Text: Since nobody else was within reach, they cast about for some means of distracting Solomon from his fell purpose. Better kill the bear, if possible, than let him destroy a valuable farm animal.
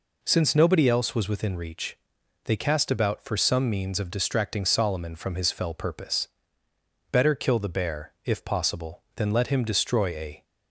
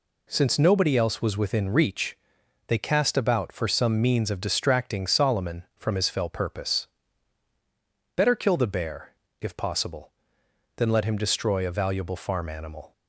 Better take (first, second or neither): second